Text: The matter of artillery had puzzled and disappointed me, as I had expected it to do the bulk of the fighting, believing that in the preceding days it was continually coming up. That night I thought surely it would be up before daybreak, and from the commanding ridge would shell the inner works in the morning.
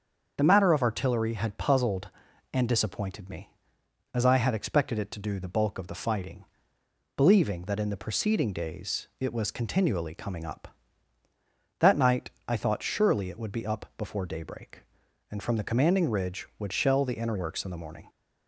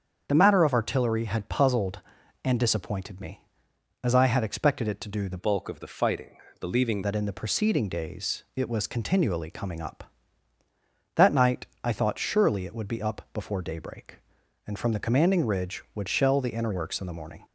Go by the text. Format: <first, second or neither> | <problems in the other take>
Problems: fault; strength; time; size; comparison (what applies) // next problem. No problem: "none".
first | starts louder than the rest; strong; until 1.2 s; 7.5 dB; also in the first // changes voice from "bulk" to "believing"; from 5.3 to 7.0 s; 1.7 s long // pauses between "night" and "I"; slight; at 11.6 s; 0.16 s long; slight in the first